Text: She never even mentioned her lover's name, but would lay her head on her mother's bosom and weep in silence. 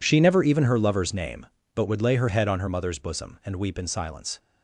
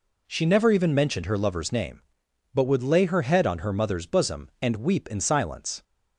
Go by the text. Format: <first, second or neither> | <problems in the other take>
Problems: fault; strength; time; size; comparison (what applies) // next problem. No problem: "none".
second | skips "mentioned"; at 0.6 s